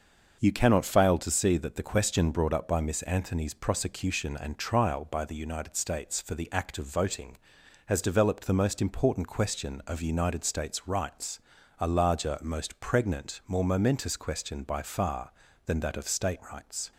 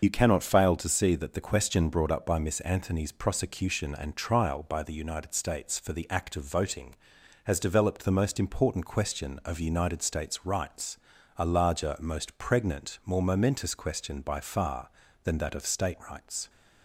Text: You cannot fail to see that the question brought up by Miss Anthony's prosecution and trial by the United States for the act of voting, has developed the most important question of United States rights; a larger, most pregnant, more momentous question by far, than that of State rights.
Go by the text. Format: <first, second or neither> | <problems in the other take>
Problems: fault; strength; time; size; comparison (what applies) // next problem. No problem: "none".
first | loses the start of "You"; at 0.0 s; 50 ms // starts louder than the rest; until 1.0 s; 6.5 dB; also in the first